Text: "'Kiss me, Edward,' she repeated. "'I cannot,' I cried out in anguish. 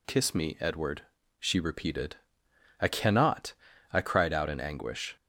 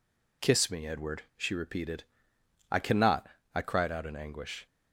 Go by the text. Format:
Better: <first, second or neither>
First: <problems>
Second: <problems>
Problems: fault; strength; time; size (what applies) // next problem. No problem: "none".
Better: neither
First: none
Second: none